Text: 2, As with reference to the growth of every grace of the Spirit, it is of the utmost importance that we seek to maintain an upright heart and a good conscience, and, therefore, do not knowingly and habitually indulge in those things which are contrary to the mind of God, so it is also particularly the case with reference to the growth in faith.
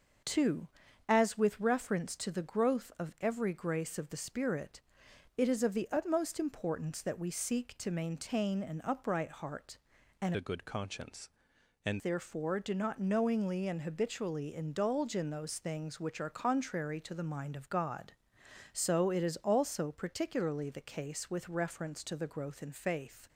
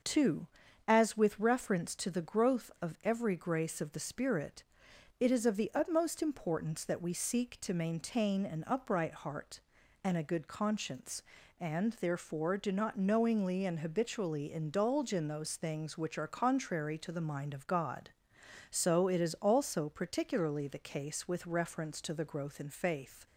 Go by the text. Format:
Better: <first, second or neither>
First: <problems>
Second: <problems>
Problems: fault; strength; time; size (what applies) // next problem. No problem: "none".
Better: second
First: changes voice from "a" to "and"; from 10.3 to 12.0 s; 1.7 s long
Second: none